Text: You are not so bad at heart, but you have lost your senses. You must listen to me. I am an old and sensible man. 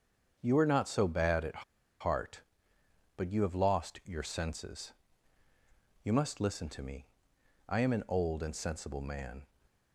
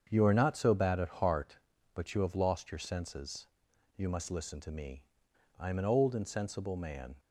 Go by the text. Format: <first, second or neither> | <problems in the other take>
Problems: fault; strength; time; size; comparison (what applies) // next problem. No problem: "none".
second | starts louder than the rest; until 1.4 s; 7 dB; strong in the second // pauses between "at" and "heart"; at 1.6 s; 0.37 s long